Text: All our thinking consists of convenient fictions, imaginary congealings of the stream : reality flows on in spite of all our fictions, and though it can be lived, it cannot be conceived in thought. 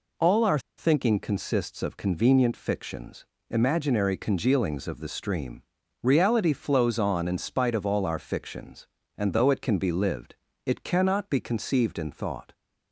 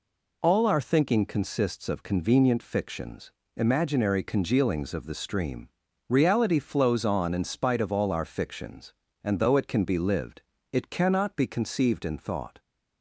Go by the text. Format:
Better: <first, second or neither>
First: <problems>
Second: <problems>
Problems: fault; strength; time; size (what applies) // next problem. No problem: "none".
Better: second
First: pauses between "our" and "thinking"; slight; at 0.5 s; 0.19 s long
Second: none